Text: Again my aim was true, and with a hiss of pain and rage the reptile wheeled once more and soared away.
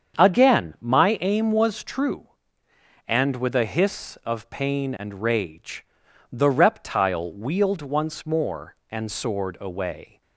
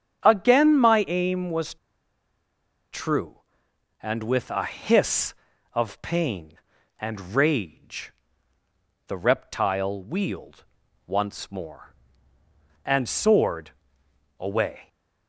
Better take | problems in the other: first | starts louder than the rest; strong; until 1.2 s; 8.5 dB; strong in the first // pauses between "was" and "true"; at 1.7 s; 1.1 s long // pauses between "rage" and "the"; noticeable; at 8.1 s; 0.96 s long; noticeable in the first // pauses between "wheeled" and "once"; at 10.6 s; 0.42 s long // pauses between "soared" and "away"; noticeable; at 13.6 s; 0.68 s long

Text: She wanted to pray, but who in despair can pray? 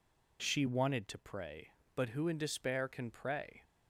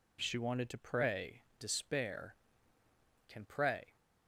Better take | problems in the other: first | skips "but who in"; at 1.5 s

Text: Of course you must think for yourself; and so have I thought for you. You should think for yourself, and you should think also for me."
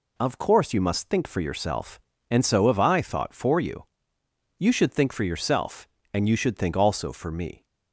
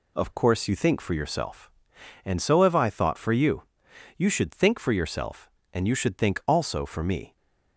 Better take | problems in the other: first | skips "must"; at 0.7 s

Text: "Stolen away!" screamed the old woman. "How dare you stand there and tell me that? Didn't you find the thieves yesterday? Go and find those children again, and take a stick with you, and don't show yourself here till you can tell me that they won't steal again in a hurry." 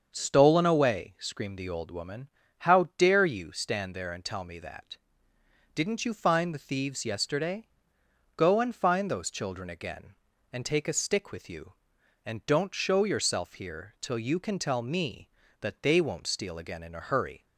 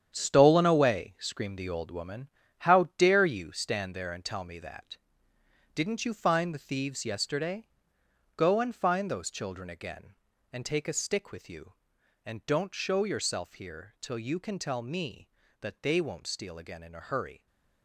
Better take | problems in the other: first | gets quieter; strong; throughout; 10 dB // starts louder than the rest; strong; until 1.1 s; 8.5 dB; also in the first

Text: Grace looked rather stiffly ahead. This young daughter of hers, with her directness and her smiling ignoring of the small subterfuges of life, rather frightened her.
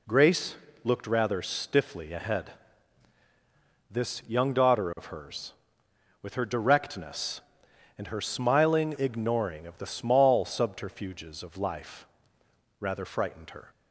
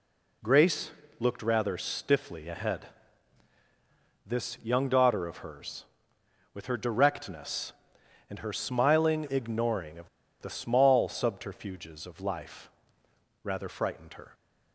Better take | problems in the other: first | pauses between "Grace" and "looked"; slight; at 0.8 s; 0.28 s long; slight in the first // pauses between "of" and "the"; slight; at 10.0 s; 0.32 s long

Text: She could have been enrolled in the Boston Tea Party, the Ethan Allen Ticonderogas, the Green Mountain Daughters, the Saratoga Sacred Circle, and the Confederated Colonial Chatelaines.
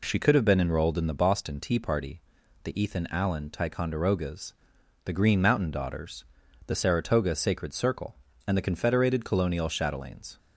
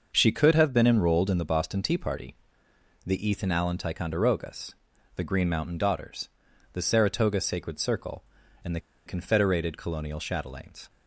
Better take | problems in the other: first | starts louder than the rest; noticeable; until 1.1 s; 6 dB // pauses between "the" and "Confederated"; slight; at 8.8 s; 0.26 s long

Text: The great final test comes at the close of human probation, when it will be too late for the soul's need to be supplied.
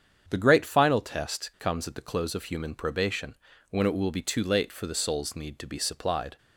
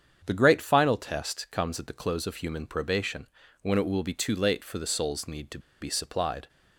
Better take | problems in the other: first | starts louder than the rest; strong; until 1.2 s; 7.5 dB; strong in the first // pauses between "to" and "be"; slight; at 5.5 s; 0.21 s long

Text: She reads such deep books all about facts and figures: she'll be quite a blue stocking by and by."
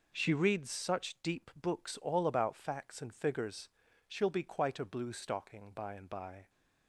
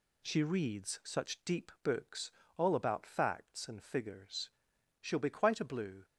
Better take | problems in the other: first | pauses between "books" and "all"; slight; at 2.3 s; 0.24 s long // stops before "stocking by and by"; at 6.0 s

